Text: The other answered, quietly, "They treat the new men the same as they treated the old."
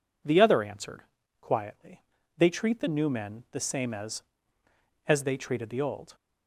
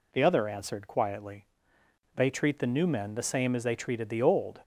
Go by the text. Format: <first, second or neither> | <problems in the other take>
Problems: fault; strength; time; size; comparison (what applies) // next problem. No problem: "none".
second | says "as" twice; at 5.0 s